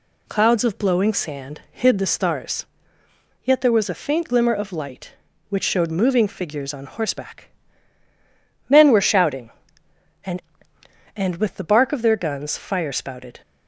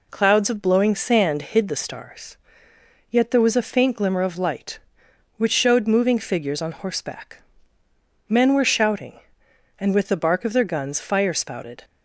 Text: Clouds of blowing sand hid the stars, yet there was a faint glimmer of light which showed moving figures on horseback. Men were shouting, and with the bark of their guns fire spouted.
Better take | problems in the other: second | says "and" twice; at 11.1 s

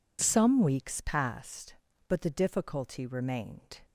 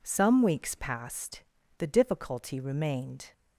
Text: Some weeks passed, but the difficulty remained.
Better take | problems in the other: first | skips "but"; at 1.5 s

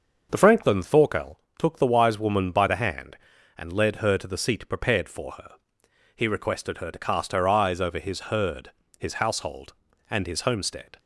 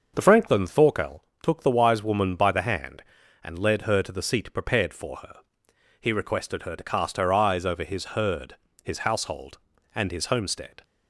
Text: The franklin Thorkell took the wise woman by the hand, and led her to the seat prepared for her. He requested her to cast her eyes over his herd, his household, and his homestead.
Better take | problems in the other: neither | starts louder than the rest; the same in both // pauses between "Thorkell" and "took"; slight; the same in both

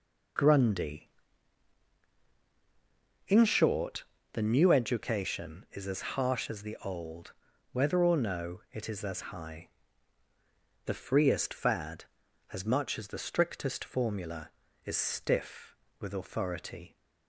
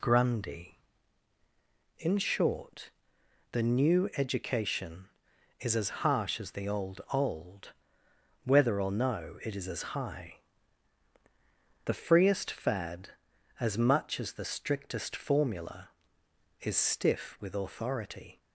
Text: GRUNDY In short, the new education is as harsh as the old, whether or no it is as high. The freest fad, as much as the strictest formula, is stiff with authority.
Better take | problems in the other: first | says "old" twice; at 7.1 s

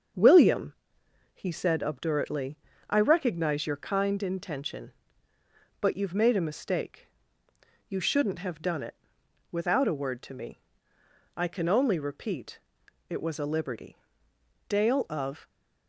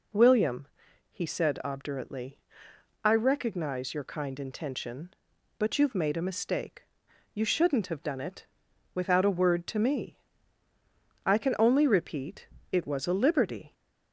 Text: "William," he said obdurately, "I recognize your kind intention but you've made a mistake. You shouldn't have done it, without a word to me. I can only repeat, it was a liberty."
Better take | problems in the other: second | starts louder than the rest; until 1.7 s; 6.5 dB // goes on to say "Dale of"; noticeable; from 14.6 s on; 0.80 s long

